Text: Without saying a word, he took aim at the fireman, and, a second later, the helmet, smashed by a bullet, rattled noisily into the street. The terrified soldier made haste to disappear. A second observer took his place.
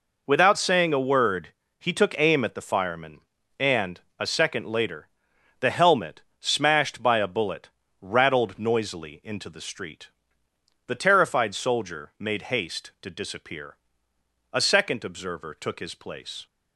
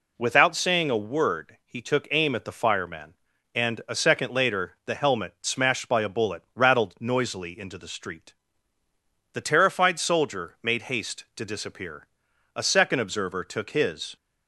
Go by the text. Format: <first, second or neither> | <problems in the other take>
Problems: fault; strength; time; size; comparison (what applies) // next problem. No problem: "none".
first | stops before "place"; at 14.1 s